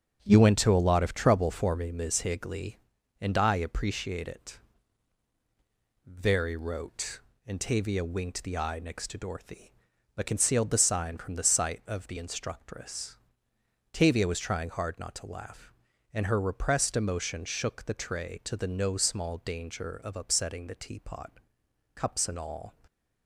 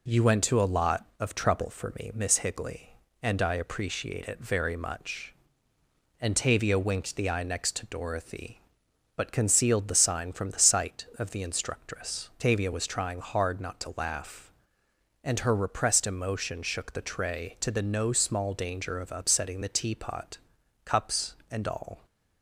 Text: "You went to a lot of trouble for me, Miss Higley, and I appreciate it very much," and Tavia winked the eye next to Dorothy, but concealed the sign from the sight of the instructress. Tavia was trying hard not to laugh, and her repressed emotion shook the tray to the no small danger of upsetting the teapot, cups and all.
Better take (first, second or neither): second